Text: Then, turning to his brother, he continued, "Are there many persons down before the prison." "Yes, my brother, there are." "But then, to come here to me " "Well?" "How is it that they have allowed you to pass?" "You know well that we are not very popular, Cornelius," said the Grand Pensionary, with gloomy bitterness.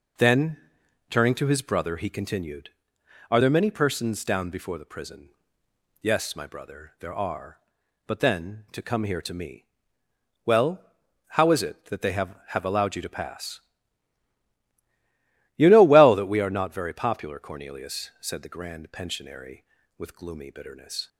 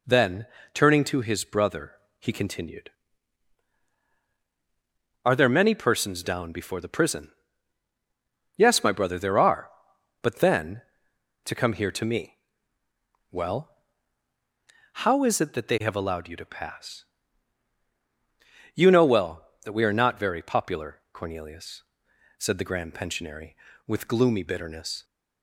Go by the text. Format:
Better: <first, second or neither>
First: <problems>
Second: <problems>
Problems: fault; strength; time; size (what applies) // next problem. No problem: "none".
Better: second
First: says "have" twice; at 12.4 s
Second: none